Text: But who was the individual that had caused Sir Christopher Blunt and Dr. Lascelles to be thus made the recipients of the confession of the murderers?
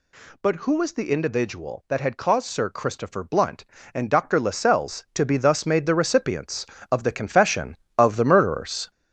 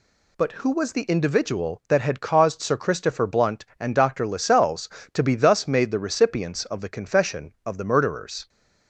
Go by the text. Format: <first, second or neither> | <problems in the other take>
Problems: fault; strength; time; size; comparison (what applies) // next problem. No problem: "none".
second | gets louder; noticeable; throughout; 5 dB